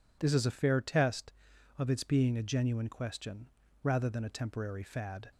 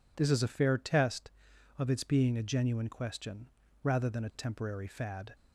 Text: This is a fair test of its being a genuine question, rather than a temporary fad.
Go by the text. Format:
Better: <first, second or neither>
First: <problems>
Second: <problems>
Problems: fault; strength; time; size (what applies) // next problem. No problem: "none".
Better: neither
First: none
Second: none